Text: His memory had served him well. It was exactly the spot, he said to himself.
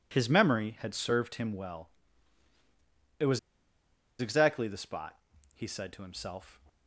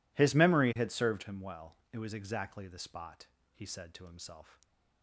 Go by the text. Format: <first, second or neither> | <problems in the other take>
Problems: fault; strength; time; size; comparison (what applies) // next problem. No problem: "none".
second | pauses between "was" and "exactly"; noticeable; at 3.3 s; 0.80 s long